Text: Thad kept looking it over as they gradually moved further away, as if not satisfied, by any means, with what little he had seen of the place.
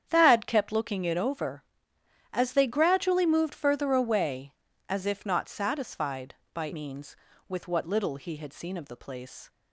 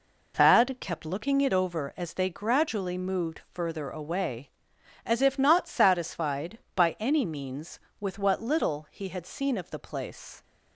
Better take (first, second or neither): second